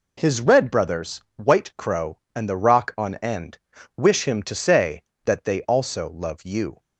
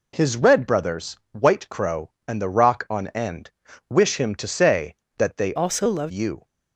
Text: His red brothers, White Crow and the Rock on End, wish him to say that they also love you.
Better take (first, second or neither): first